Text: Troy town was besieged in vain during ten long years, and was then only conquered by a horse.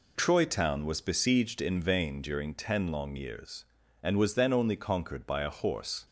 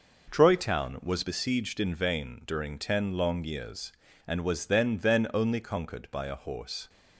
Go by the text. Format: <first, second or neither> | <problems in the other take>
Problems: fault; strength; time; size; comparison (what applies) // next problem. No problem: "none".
first | says "then" twice; at 4.9 s